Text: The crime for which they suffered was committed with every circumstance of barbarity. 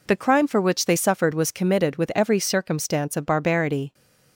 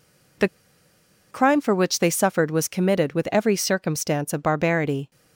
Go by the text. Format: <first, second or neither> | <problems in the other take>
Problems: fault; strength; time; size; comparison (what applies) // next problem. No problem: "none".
first | pauses between "The" and "crime"; noticeable; at 0.4 s; 0.83 s long